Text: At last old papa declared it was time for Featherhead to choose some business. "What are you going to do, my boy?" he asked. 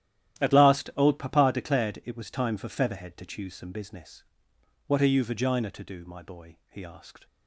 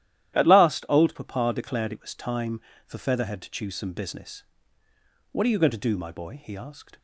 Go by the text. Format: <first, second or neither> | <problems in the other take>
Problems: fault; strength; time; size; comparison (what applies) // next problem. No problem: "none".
second | starts louder than the rest; strong; until 1.4 s; 12 dB; strong in the second // says "vagina" for "going"; at 5.2 s